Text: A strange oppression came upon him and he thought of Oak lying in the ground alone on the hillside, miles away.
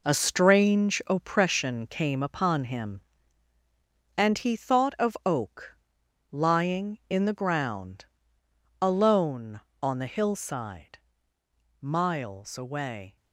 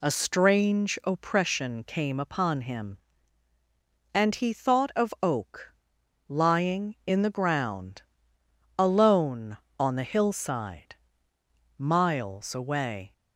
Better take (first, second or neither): second